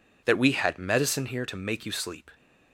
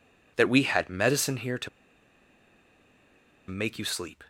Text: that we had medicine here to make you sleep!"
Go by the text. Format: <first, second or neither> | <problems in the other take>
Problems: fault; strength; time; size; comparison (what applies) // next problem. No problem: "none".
first | pauses between "to" and "make"; strong; at 1.6 s; 1.7 s long